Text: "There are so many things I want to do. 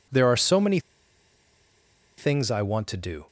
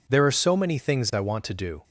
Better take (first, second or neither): second